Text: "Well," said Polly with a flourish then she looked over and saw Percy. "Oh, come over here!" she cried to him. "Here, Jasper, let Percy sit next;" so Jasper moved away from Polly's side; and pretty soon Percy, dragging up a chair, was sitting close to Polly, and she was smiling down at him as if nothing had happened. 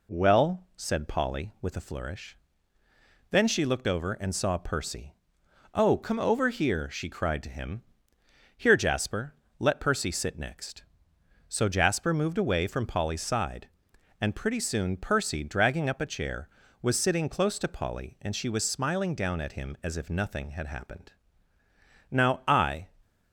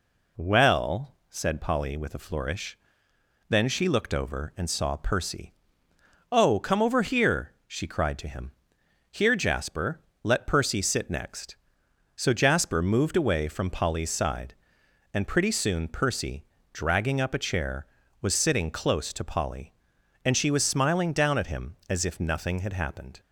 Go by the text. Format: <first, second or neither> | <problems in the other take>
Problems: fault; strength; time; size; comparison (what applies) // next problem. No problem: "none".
second | pauses between "flourish" and "then"; noticeable; at 2.3 s; 0.94 s long; noticeable in the second // goes on to say "Now I"; noticeable; from 22.0 s on; 0.78 s long